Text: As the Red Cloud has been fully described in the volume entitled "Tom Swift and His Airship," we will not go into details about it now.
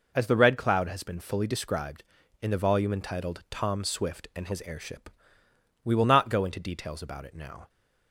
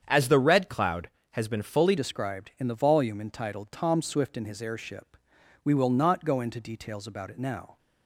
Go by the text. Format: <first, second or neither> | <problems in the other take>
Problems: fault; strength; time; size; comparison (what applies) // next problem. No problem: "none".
first | starts louder than the rest; strong; until 1.0 s; 8 dB // changes voice at "described"; from 1.9 s on; 5.8 s long